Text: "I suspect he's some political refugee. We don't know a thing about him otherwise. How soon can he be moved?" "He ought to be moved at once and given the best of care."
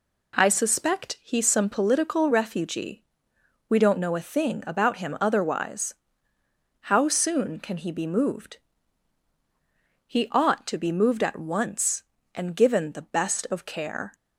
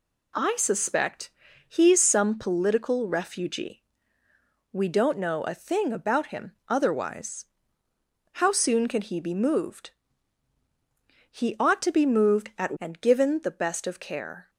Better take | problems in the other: first | pauses between "suspect" and "he's"; at 1.3 s; 0.38 s long // skips "once"; at 12.7 s

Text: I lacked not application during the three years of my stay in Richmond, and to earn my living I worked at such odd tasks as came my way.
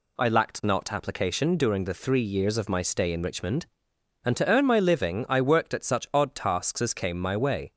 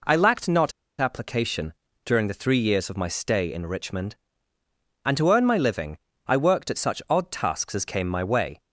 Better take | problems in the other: first | pauses between "not" and "application"; slight; at 0.7 s; 0.28 s long // pauses between "application" and "during"; slight; at 1.7 s; 0.34 s long // pauses between "living" and "I"; slight; at 5.9 s; 0.30 s long

